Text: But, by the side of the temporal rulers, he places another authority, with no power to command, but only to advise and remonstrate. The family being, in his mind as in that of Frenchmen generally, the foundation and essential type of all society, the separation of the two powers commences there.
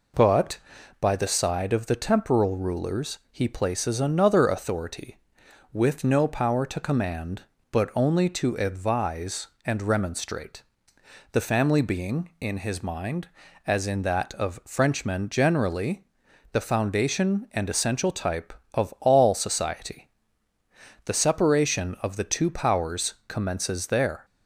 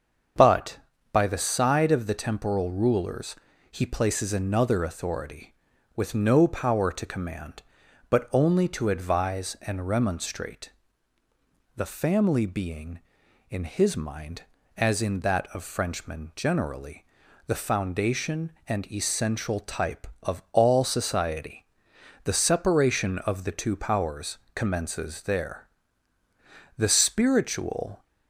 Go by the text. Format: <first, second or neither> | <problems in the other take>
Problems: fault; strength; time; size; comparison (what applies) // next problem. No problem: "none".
first | starts louder than the rest; until 1.7 s; 7 dB // pauses between "powers" and "commences"; slight; at 24.3 s; 0.16 s long // goes on to say "The spiritual"; noticeable; from 26.7 s on; 1.2 s long